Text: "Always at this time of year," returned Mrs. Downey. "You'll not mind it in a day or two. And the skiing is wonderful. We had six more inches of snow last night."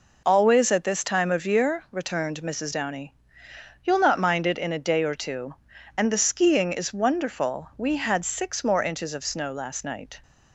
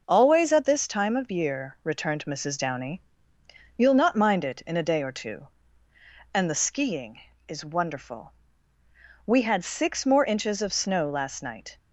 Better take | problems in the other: neither | none

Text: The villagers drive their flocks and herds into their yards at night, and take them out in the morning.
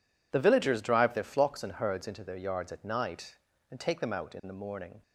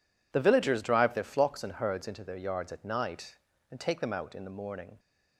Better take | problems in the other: neither | none

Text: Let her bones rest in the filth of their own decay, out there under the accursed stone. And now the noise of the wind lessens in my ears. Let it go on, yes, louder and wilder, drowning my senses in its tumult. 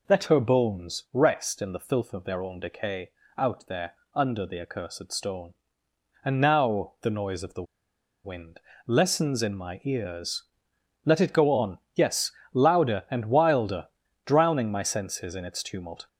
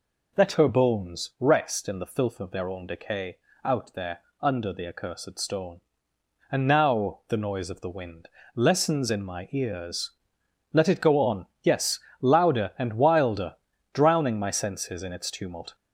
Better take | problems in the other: second | pauses between "there" and "under"; slight; at 3.9 s; 0.18 s long; slight in the second // pauses between "the" and "wind"; noticeable; at 7.6 s; 0.61 s long // pauses between "wind" and "lessens"; slight; at 8.5 s; 0.28 s long; slight in the second

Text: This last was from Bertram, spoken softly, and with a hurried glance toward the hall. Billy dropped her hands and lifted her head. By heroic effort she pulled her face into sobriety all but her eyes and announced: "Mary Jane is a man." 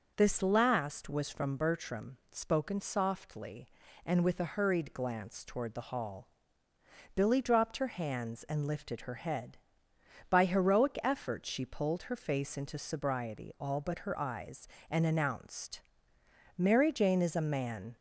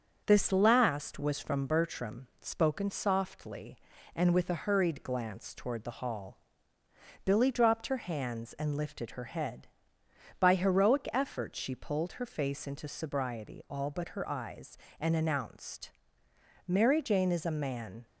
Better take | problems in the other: first | gets quieter; slight; throughout; 2 dB

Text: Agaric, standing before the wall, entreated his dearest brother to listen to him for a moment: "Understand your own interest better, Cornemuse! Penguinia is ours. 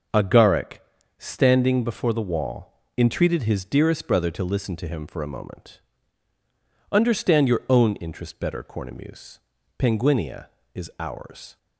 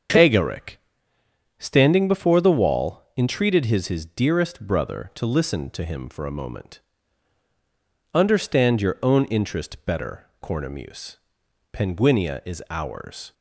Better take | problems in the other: first | starts louder than the rest; until 1.9 s; 7 dB; also in the first // says "his" twice; at 3.8 s

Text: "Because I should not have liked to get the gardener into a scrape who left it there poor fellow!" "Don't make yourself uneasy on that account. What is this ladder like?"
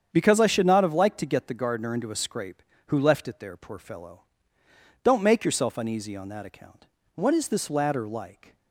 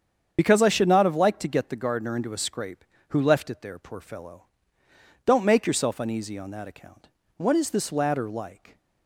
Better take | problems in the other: first | loses the start of "Because"; at 0.3 s; 35 ms // starts louder than the rest; strong; until 1.3 s; 7.5 dB; strong in the first

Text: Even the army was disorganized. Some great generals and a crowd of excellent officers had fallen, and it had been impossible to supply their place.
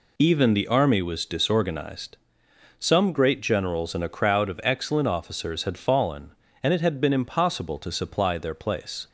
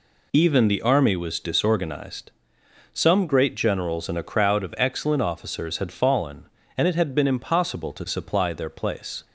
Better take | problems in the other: neither | none

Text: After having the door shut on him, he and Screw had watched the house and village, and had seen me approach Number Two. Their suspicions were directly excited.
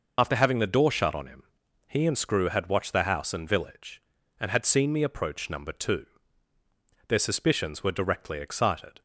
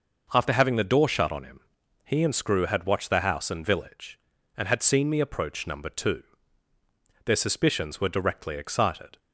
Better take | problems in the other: second | loses the start of "After"; at 0.1 s; 60 ms

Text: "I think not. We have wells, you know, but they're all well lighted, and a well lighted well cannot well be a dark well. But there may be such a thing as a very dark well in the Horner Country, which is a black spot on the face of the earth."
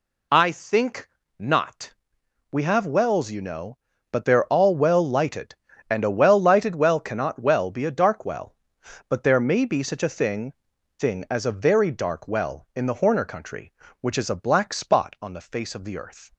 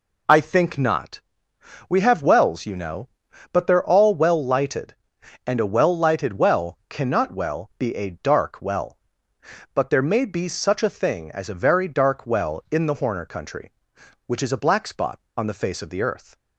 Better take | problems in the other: second | pauses between "think" and "not"; slight; at 1.0 s; 0.30 s long // says "thing" twice; at 10.9 s

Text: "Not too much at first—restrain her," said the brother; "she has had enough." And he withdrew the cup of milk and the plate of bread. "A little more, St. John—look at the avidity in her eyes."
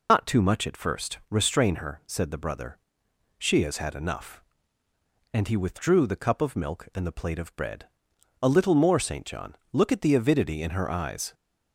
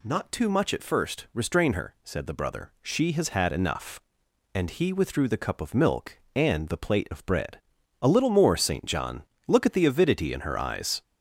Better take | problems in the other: second | loses the start of "Not"; at 0.0 s; 115 ms

